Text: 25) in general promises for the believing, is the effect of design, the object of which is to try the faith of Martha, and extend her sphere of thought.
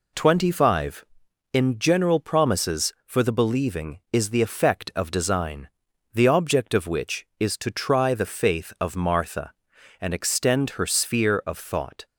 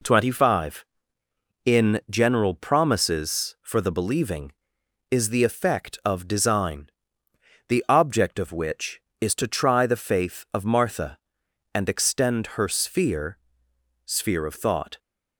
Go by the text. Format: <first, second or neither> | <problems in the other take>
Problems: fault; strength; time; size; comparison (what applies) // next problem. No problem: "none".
first | says "sphere" twice; at 14.0 s